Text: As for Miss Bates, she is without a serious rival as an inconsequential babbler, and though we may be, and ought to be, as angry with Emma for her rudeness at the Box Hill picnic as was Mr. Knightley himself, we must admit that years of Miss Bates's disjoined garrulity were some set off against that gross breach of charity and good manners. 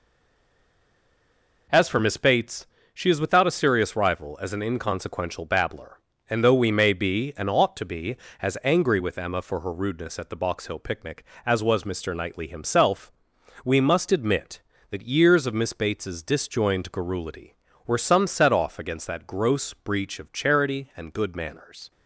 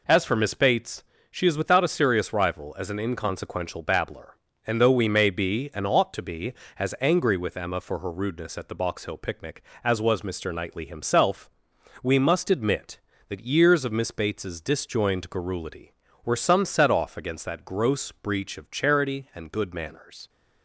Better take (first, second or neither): second